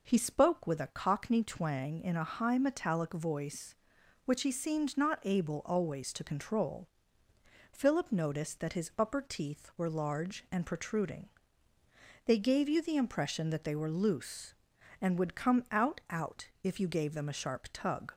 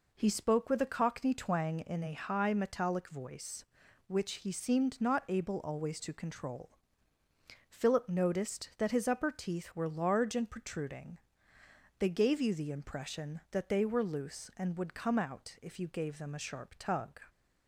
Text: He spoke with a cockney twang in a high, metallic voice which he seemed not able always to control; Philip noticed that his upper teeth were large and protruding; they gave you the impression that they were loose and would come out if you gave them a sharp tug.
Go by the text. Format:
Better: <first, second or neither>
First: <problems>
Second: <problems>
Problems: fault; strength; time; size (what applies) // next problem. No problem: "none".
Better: second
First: says "out" twice; at 16.0 s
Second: none